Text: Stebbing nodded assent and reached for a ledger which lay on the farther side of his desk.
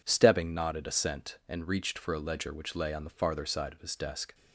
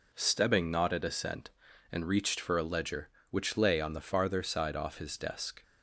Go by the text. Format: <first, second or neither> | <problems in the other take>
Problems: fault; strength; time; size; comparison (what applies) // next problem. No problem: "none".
first | says "off" for "of"; at 4.7 s